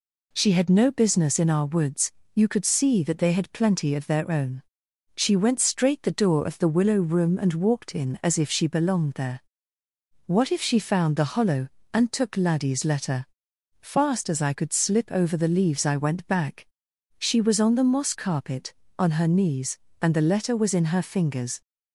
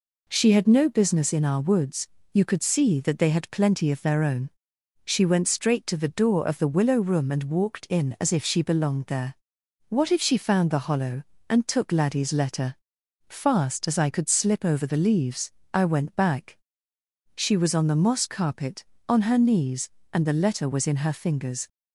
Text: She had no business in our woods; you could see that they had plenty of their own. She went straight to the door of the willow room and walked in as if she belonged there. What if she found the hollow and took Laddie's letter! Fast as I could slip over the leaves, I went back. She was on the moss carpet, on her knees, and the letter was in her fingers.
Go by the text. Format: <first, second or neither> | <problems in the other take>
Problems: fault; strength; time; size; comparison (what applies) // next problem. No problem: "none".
second | skips "to"; at 6.0 s